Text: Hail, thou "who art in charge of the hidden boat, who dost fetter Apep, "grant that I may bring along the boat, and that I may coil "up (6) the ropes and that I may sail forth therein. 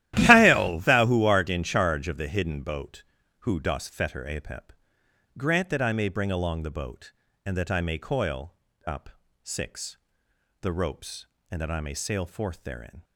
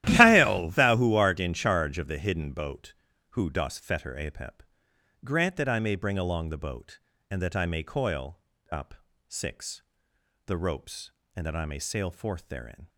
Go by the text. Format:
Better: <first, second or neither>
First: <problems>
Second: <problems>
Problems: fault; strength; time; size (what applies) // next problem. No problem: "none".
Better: neither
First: starts louder than the rest; strong; until 1.1 s; 13.5 dB // pauses between "coil" and "up"; slight; at 8.5 s; 0.34 s long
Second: starts louder than the rest; strong; until 1.0 s; 13.5 dB // pauses between "coil" and "up"; slight; at 8.3 s; 0.34 s long